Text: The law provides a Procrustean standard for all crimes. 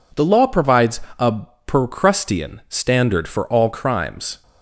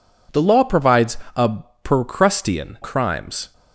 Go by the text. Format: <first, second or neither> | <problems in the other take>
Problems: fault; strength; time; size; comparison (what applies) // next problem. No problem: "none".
first | pauses between "provides" and "a"; slight; at 1.1 s; 0.20 s long; slight in the first // pauses between "a" and "Procrustean"; slight; at 1.5 s; 0.24 s long; slight in the first // skips "standard for all"; at 2.7 s